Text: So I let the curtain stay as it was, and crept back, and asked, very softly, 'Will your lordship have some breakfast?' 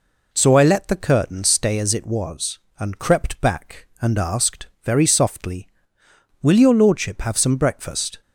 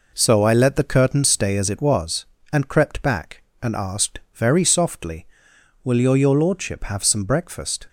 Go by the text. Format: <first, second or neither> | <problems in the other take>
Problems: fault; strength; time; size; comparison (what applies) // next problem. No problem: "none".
first | says "your" twice; at 6.1 s